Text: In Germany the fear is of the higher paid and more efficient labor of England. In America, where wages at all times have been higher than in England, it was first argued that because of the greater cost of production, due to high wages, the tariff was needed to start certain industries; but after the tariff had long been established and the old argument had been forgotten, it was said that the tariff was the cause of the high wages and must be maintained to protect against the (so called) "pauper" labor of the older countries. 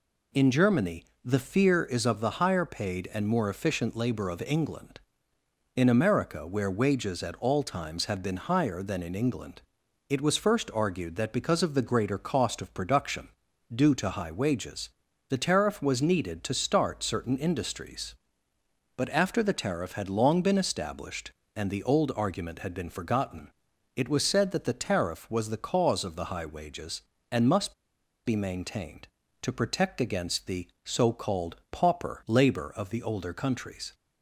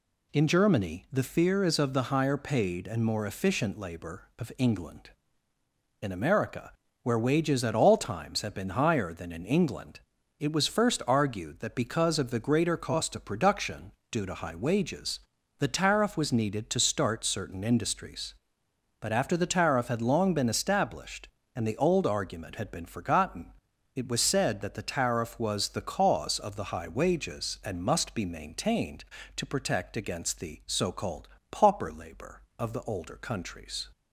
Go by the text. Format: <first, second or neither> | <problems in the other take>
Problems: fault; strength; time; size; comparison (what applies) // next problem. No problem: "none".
second | pauses between "Germany" and "the"; slight; at 1.0 s; 0.18 s long // pauses between "must" and "be"; noticeable; at 27.7 s; 0.51 s long